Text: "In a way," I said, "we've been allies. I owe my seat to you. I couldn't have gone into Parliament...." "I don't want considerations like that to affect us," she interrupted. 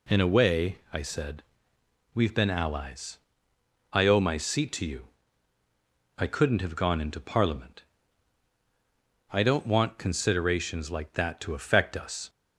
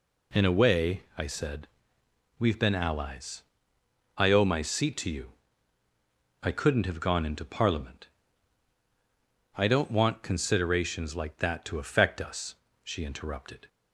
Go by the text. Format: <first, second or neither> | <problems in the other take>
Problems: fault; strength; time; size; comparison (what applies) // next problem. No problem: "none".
second | stops before "she interrupted"; at 12.2 s